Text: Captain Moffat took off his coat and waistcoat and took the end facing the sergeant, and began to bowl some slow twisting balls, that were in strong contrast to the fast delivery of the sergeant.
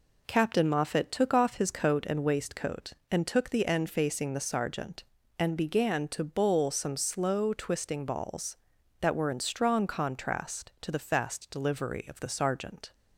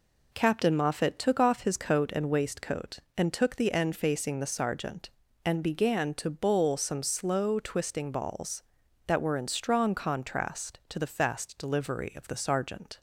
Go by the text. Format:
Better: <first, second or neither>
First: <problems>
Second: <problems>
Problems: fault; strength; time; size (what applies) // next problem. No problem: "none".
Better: neither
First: none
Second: none